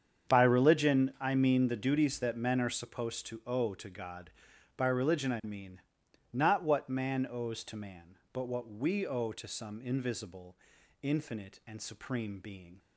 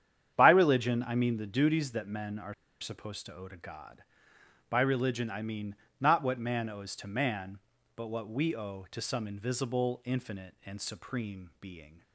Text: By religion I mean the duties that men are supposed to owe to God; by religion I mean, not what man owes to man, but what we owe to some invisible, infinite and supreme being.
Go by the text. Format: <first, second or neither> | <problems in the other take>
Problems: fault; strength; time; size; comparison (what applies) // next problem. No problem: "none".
first | starts louder than the rest; strong; until 1.3 s; 9 dB; strong in the first // pauses between "are" and "supposed"; slight; at 2.5 s; 0.27 s long